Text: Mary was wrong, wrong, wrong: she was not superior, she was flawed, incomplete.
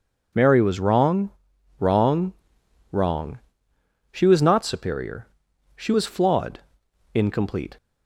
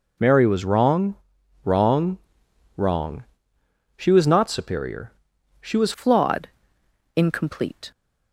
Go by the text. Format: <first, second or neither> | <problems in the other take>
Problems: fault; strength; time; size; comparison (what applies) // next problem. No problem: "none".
first | changes voice at "flawed"; from 5.9 s on; 2.0 s long